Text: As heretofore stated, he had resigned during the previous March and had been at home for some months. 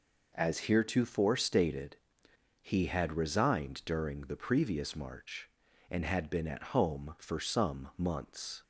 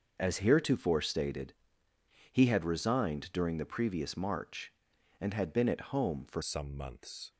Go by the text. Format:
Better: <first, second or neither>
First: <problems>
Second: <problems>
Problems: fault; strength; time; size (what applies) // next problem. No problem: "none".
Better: first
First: none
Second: starts louder than the rest; noticeable; until 1.2 s; 6 dB // changes voice at "some"; from 6.4 s on; 0.9 s long